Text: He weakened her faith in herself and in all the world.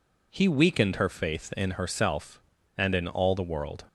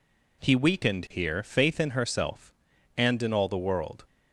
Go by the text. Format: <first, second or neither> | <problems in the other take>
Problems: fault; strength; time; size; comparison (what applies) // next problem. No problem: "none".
first | says "here" for "her"; at 1.1 s